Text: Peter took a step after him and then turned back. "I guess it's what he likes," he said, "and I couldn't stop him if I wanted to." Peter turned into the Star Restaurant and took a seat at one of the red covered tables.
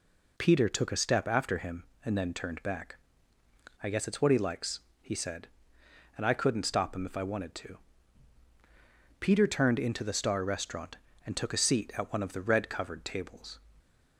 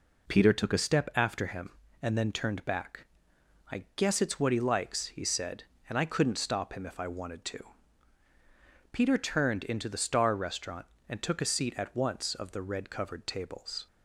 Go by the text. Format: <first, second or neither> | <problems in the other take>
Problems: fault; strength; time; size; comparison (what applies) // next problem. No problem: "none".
first | says "once" for "one"; at 11.9 s